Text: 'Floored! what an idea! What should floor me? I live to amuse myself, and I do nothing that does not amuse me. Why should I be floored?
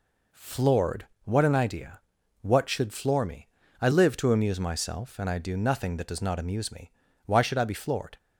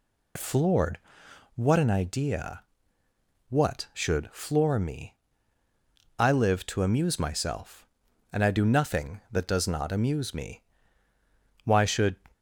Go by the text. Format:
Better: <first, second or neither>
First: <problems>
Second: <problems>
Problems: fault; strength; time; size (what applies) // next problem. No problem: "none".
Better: first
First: none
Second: stops before "I be floored"; at 12.3 s